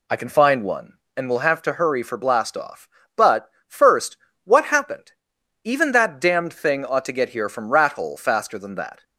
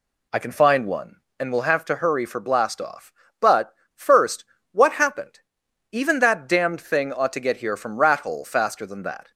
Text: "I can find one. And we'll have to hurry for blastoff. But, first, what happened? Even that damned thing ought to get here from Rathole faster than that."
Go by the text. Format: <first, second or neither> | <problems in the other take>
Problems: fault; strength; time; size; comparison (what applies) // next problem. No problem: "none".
neither | none